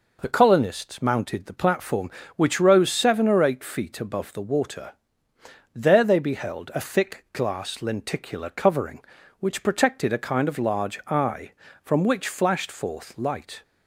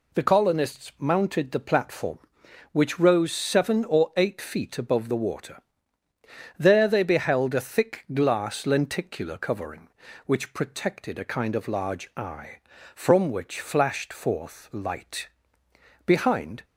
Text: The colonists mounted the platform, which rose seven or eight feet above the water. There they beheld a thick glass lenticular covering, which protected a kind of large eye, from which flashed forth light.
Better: first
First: none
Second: goes on to say "Behind"; from 16.0 s on; 0.58 s long

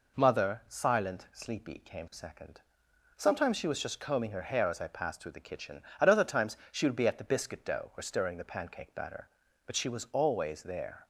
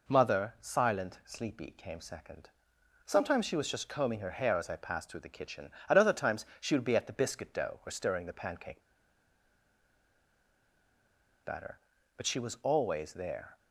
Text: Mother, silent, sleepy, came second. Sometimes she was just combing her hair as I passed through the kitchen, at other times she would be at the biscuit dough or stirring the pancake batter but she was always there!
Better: first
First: none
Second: pauses between "pancake" and "batter"; strong; at 8.8 s; 2.6 s long

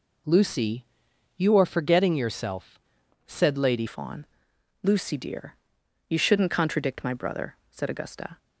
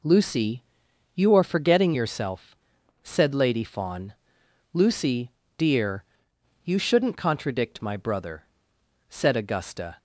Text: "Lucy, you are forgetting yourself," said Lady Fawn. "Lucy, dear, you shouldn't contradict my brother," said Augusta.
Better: second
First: changes voice at "Fawn"; from 3.8 s on; 4.5 s long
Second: none

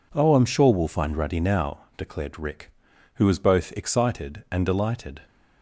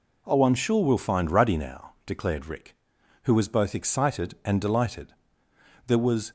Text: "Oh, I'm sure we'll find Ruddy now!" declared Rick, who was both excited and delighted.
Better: first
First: none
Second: goes on to say "There was"; slight; from 5.8 s on; 0.44 s long

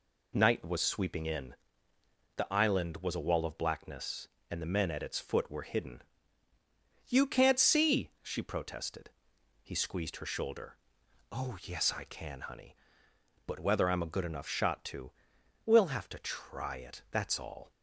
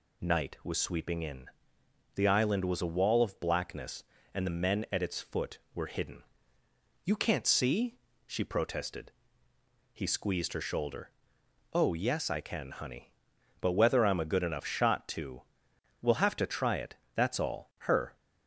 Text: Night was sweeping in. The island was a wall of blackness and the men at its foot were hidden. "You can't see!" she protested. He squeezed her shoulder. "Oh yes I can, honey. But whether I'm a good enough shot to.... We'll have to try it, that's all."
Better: first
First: none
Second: goes on to say "Her"; slight; from 17.8 s on; 0.34 s long

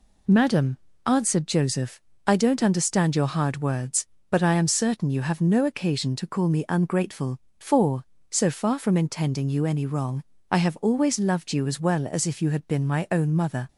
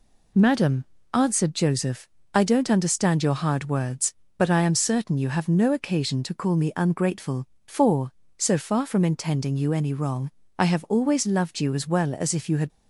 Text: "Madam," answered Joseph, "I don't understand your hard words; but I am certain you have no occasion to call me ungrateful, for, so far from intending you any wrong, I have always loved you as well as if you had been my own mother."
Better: first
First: none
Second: stops before "been my own mother"; at 12.7 s

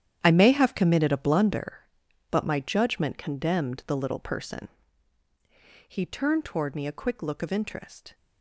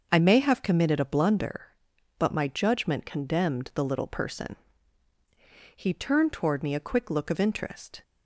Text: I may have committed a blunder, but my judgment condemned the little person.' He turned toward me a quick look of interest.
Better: second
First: gets quieter; strong; throughout; 13.5 dB // starts louder than the rest; strong; until 1.2 s; 10 dB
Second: starts louder than the rest; until 1.1 s; 6 dB

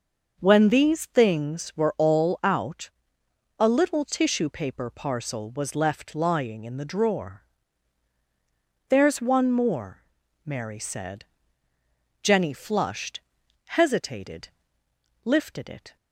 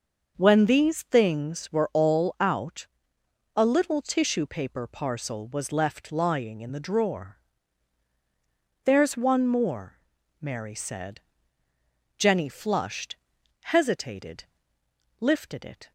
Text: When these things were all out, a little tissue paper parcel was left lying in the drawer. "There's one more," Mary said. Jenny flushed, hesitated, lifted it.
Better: neither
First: starts louder than the rest; until 1.4 s; 6 dB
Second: starts louder than the rest; until 1.3 s; 6 dB

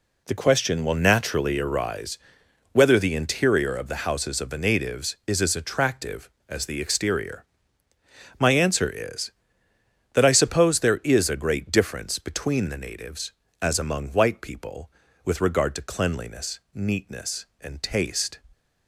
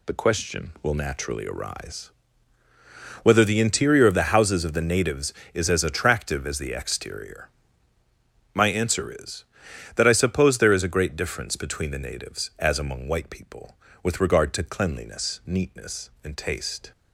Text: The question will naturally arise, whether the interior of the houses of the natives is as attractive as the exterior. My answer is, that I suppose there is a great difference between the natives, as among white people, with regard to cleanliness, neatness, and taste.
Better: neither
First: none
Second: none

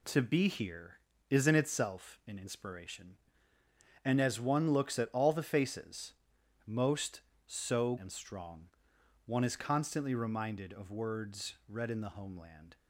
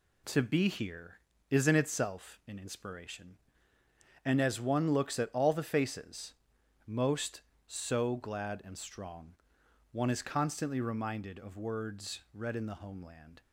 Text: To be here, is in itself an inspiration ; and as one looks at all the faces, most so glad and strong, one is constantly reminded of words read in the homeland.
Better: second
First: skips "glad"; at 7.9 s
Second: none

